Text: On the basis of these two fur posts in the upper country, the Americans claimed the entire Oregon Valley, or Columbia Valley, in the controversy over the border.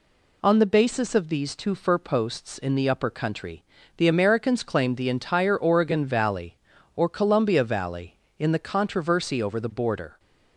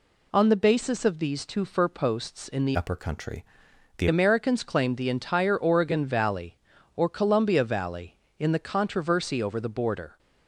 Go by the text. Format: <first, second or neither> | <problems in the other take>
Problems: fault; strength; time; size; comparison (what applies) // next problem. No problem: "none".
first | changes voice from "upper" to "the"; from 2.7 to 4.0 s; 1.3 s long